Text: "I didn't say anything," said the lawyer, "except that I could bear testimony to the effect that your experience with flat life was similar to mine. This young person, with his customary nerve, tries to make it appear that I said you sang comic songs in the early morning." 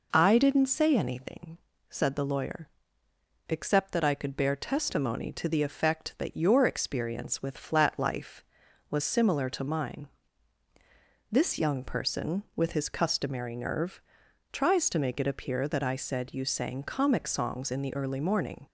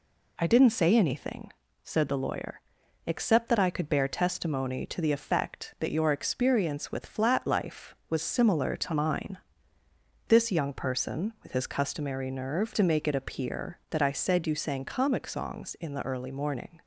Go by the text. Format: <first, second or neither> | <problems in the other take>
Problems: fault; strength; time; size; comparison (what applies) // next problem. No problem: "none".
first | skips "tries"; at 12.7 s